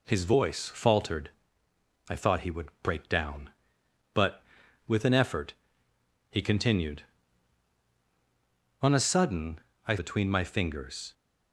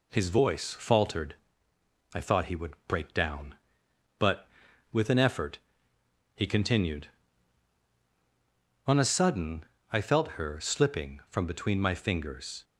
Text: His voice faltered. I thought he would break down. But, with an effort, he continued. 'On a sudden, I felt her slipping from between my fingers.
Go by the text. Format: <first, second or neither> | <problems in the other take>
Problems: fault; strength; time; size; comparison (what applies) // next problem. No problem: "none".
second | skips "felt her slipping from"; at 9.9 s